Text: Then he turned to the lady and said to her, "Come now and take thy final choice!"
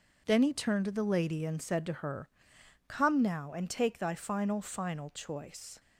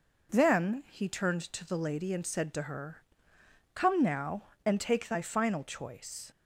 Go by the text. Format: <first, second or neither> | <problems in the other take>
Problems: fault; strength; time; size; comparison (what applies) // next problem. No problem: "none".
second | says "final" twice; at 4.6 s